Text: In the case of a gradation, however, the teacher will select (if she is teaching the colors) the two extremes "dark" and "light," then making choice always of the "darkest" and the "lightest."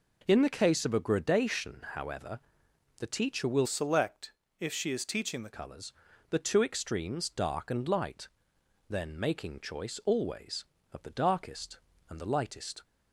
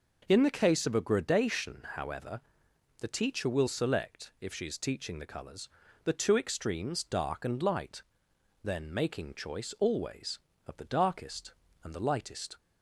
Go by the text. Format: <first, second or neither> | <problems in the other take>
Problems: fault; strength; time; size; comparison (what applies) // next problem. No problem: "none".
second | changes voice from "select" to "the"; from 3.6 to 5.5 s; 1.9 s long